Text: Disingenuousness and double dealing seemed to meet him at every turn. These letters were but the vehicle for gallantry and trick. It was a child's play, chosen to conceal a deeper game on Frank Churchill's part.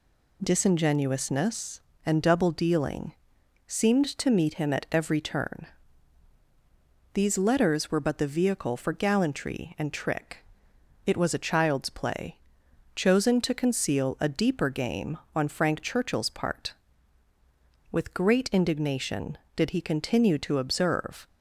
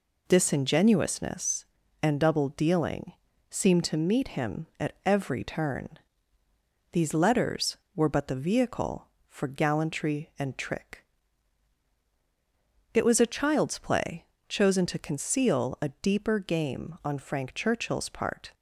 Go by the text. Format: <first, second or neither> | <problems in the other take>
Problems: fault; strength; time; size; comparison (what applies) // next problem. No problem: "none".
second | pauses between "dealing" and "seemed"; noticeable; at 3.1 s; 0.54 s long; also in the second // goes on to say "With great indignation did he continue to observe"; strong; from 17.9 s on; 3.3 s long